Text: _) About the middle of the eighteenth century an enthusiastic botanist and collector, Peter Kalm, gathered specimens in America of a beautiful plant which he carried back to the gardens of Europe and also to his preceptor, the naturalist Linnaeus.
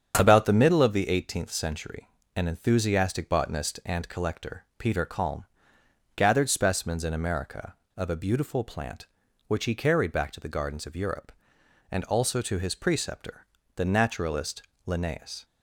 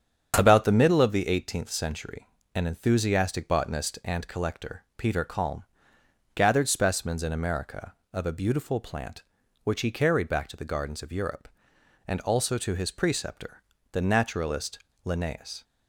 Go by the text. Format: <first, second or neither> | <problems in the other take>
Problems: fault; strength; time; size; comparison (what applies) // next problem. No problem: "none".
neither | starts louder than the rest; strong; the same in both // pauses between "century" and "an"; slight; the same in both // pauses between "naturalist" and "Linnaeus"; slight; the same in both